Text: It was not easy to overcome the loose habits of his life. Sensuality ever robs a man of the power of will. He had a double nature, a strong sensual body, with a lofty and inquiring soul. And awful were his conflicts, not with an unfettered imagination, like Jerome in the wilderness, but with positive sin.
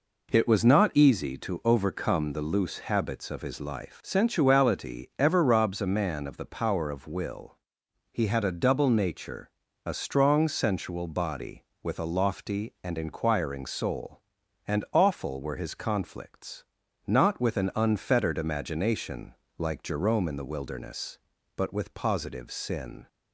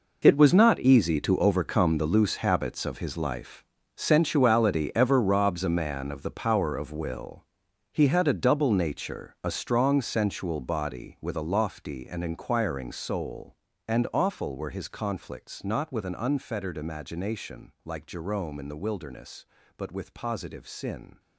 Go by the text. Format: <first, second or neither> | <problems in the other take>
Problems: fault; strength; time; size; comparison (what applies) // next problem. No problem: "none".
first | gets quieter; strong; throughout; 14 dB